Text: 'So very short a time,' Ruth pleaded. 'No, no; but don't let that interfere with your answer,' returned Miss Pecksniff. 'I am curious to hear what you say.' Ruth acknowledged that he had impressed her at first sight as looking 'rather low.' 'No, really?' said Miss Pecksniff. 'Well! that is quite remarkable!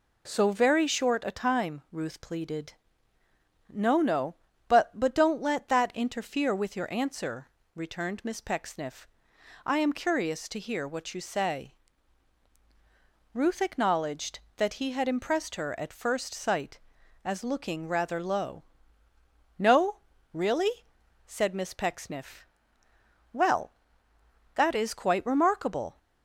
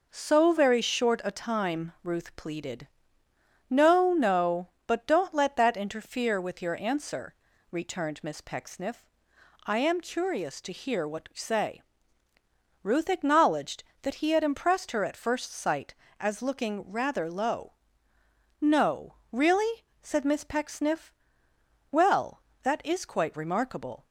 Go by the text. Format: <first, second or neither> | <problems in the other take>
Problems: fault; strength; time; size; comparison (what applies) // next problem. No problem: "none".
second | says "but" twice; at 4.9 s